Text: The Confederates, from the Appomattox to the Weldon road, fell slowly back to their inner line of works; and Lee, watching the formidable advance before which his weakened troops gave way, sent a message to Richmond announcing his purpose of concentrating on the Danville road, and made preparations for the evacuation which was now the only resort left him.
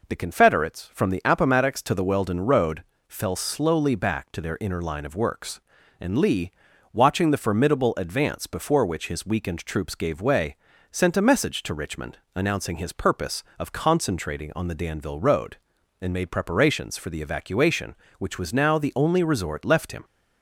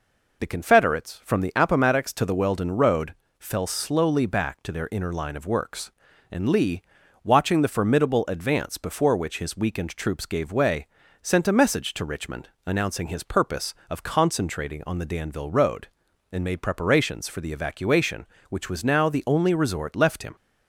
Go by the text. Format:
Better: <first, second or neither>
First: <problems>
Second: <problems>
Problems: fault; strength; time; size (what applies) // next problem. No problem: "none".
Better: first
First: pauses between "Richmond" and "announcing"; slight; at 12.1 s; 0.16 s long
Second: loses the start of "The"; at 0.3 s; 45 ms // pauses between "Richmond" and "announcing"; slight; at 12.4 s; 0.16 s long